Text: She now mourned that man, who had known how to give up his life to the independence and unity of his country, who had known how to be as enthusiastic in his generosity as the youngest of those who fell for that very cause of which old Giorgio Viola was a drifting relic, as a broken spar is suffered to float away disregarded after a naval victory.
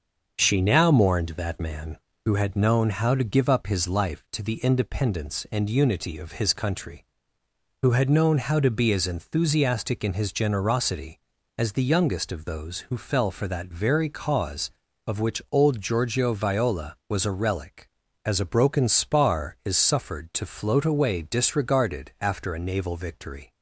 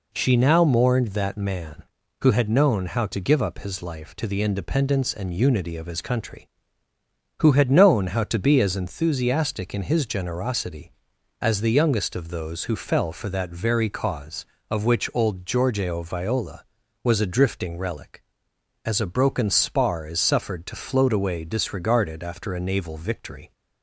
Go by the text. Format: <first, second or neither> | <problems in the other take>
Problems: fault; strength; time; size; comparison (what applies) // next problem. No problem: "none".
second | starts louder than the rest; until 1.3 s; 6.5 dB // skips "drifting"; at 17.3 s